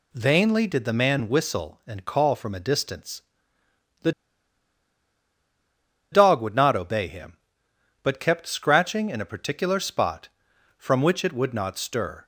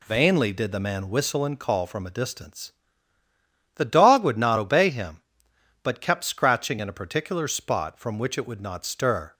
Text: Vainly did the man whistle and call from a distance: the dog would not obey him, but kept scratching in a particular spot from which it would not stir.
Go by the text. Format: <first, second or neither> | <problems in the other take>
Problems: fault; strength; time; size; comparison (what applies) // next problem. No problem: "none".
second | pauses between "the" and "dog"; strong; at 4.1 s; 2.0 s long